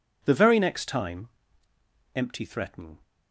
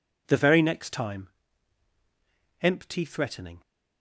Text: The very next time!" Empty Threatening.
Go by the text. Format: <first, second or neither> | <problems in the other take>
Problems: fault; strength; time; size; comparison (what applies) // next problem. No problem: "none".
neither | none